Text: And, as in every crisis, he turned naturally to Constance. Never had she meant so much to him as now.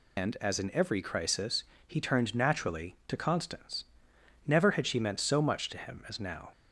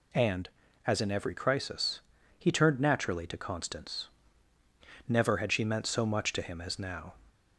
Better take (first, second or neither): second